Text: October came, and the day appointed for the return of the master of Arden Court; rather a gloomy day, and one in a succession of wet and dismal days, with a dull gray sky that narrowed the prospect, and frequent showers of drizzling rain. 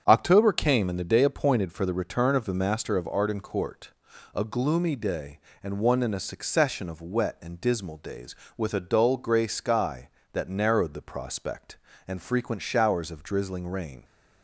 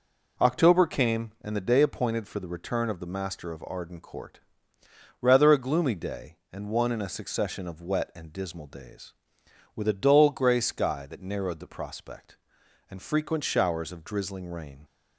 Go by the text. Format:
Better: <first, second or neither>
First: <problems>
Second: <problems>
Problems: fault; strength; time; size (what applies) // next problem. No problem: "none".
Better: second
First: starts louder than the rest; strong; until 1.0 s; 7.5 dB // skips "rather"; at 4.1 s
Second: none